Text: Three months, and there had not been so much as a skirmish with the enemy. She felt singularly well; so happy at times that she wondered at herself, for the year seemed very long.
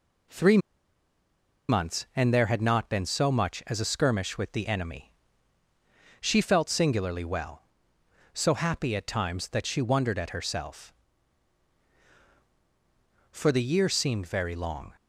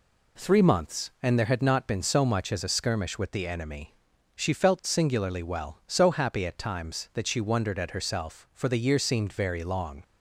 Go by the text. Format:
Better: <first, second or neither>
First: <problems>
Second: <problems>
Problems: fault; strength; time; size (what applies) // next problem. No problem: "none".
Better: second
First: pauses between "Three" and "months"; at 0.5 s; 1.1 s long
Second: none